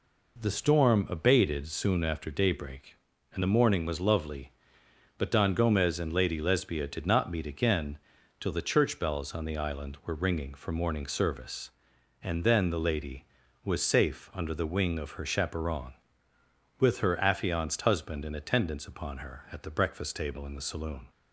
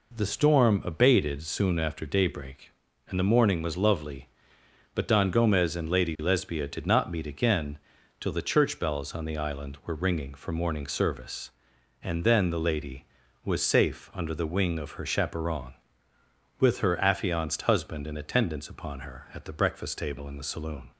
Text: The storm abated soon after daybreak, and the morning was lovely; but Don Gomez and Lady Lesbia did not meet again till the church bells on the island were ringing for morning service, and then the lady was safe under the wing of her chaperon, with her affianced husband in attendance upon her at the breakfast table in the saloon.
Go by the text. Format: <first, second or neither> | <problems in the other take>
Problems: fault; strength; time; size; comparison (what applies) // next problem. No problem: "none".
neither | pauses between "again" and "till"; the same in both